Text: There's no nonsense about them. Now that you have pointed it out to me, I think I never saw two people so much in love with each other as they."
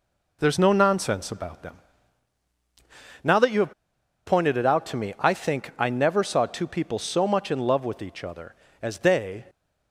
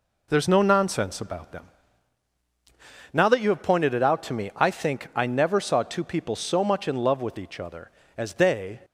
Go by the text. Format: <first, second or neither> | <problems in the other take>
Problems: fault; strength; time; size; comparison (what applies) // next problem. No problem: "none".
second | pauses between "have" and "pointed"; noticeable; at 3.7 s; 0.52 s long